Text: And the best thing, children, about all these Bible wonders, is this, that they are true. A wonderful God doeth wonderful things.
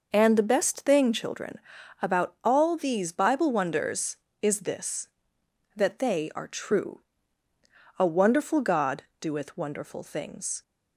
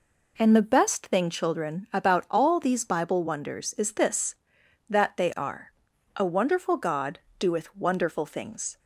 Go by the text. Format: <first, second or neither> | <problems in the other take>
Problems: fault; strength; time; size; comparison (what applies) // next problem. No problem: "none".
first | skips "true"; at 5.9 s // pauses between "God" and "doeth"; slight; at 7.1 s; 0.20 s long; slight in the first